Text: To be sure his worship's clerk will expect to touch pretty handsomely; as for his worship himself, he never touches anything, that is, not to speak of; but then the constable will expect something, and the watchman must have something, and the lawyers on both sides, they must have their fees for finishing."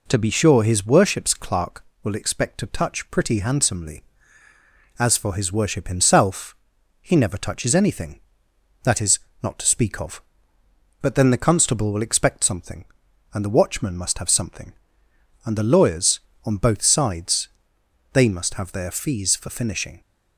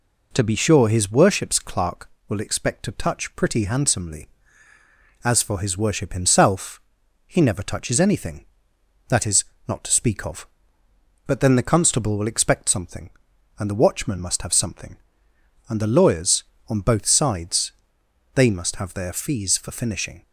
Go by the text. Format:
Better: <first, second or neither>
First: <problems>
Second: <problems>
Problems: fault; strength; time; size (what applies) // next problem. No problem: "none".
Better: neither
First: none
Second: none